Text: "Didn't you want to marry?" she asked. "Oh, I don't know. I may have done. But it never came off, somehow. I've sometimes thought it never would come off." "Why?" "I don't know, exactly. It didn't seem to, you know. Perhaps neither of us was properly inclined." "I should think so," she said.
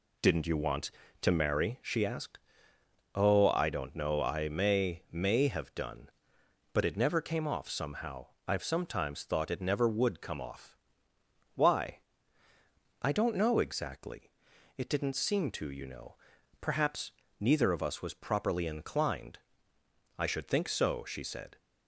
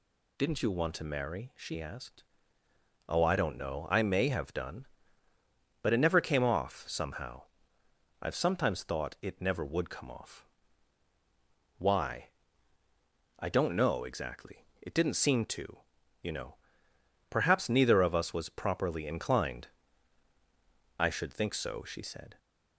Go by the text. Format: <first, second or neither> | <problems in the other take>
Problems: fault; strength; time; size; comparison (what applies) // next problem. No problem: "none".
second | says "may" twice; at 5.1 s // pauses between "Perhaps" and "neither"; slight; at 17.1 s; 0.26 s long